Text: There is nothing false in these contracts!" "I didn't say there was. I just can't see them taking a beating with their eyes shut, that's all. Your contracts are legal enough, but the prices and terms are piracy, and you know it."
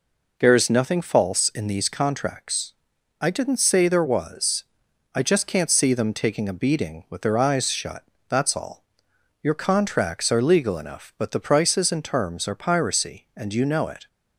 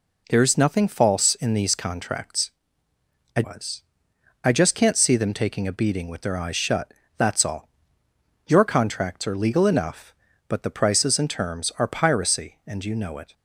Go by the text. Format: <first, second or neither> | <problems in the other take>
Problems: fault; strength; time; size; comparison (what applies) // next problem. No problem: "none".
first | skips "didn't say there"; at 3.4 s